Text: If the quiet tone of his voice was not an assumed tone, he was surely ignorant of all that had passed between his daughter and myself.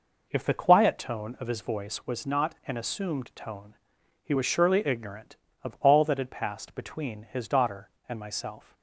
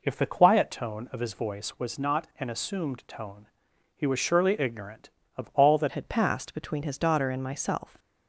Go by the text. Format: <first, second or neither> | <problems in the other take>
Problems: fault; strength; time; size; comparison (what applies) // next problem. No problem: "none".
first | changes voice at "had"; from 5.9 s on; 2.0 s long